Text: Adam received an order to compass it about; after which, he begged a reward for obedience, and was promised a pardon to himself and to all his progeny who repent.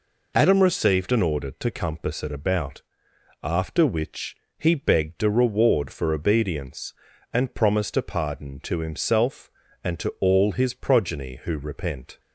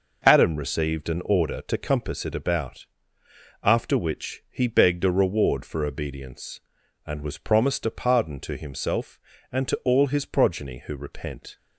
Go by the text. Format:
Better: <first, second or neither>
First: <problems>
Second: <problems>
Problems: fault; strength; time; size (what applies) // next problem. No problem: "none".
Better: second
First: skips "was"; at 7.5 s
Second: none